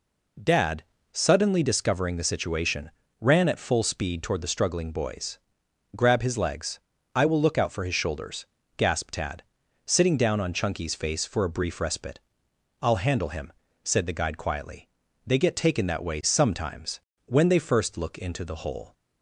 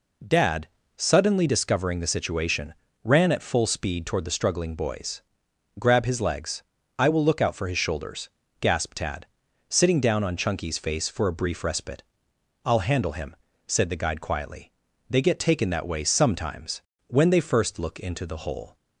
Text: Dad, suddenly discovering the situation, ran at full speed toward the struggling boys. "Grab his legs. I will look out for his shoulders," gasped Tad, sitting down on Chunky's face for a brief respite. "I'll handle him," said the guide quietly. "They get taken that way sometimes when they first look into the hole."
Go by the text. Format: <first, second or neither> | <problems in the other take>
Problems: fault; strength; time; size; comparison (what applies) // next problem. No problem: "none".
neither | pauses between "sometimes" and "when"; slight; the same in both